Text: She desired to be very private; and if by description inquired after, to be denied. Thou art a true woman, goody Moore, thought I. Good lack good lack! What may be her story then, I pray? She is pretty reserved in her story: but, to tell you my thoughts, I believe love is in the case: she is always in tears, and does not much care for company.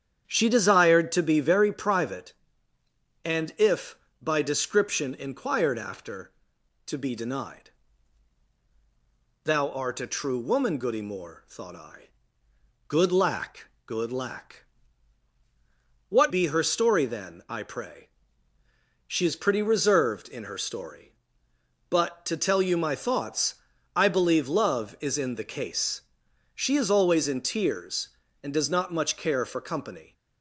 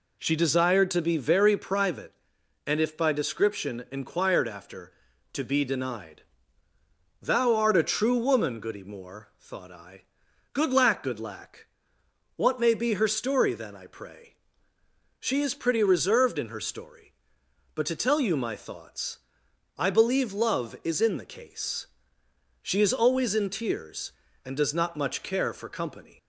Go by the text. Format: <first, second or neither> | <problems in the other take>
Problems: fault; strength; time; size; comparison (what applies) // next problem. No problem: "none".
second | starts louder than the rest; strong; until 1.2 s; 8.5 dB // pauses between "lack" and "good"; slight; at 13.6 s; 0.20 s long // skips "may"; at 16.3 s